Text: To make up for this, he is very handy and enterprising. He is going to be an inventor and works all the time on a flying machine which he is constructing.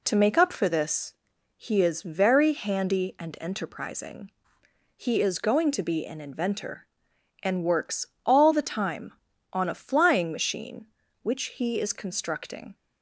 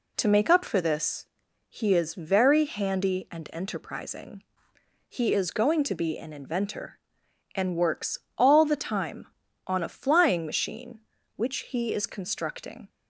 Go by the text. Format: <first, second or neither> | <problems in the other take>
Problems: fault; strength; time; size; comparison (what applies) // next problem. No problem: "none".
neither | pauses between "works" and "all"; slight; the same in both